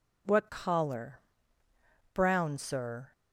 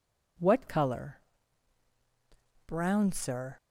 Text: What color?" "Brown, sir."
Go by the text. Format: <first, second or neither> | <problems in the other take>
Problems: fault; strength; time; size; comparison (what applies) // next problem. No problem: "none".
second | says "collar" for "color"; at 0.5 s